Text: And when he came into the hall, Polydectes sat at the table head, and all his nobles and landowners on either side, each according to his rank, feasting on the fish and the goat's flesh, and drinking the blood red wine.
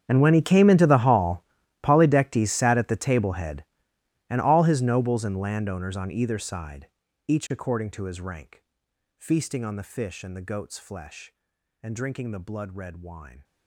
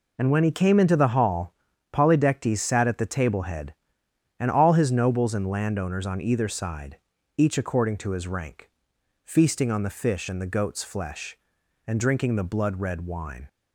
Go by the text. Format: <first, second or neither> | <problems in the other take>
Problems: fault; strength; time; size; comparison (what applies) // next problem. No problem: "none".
second | gets quieter; strong; throughout; 20.5 dB